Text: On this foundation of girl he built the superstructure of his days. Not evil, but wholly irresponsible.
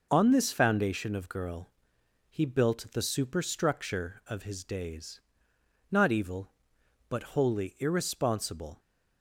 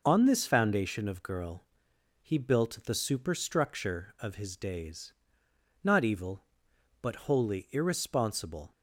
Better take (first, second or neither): neither